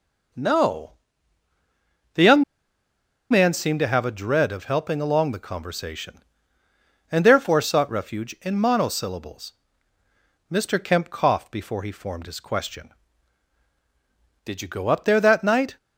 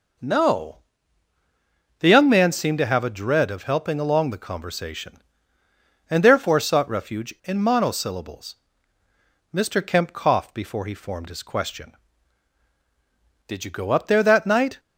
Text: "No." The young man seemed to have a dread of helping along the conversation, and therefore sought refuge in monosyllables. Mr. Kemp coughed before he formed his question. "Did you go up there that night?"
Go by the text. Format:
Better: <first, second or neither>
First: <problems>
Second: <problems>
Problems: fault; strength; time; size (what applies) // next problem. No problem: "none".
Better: second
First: pauses between "young" and "man"; noticeable; at 2.4 s; 0.88 s long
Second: none